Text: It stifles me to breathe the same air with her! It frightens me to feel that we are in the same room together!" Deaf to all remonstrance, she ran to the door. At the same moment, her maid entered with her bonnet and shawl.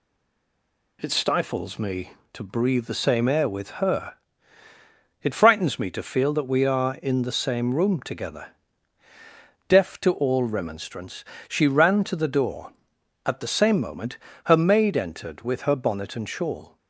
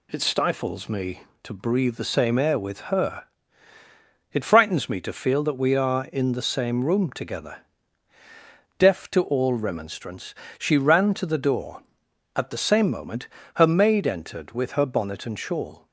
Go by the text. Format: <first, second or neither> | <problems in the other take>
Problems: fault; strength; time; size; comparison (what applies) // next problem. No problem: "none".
second | stays silent before the first word; until 1.0 s; 1.0 s long